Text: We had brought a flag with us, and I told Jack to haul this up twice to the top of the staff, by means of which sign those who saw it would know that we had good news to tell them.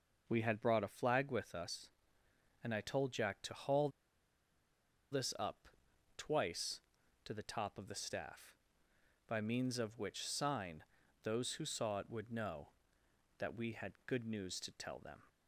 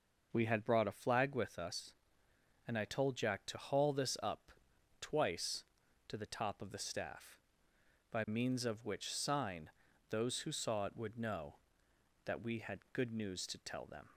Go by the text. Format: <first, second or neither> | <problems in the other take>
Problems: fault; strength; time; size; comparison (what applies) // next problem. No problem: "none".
second | pauses between "haul" and "this"; at 3.8 s; 1.2 s long // pauses between "up" and "twice"; noticeable; at 5.6 s; 0.48 s long; noticeable in the second // pauses between "sign" and "those"; at 10.8 s; 0.40 s long; also in the second